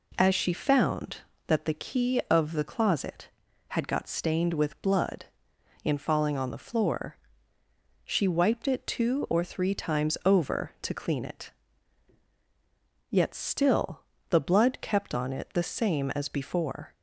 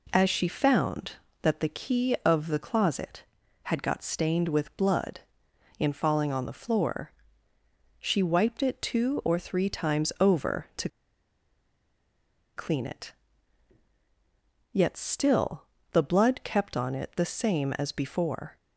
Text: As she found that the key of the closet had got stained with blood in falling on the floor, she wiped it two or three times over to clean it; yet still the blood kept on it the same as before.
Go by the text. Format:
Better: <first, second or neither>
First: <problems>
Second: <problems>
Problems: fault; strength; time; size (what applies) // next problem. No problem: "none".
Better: first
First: pauses between "still" and "the"; slight; at 14.0 s; 0.26 s long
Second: pauses between "to" and "clean"; strong; at 10.8 s; 1.6 s long // pauses between "still" and "the"; slight; at 15.6 s; 0.26 s long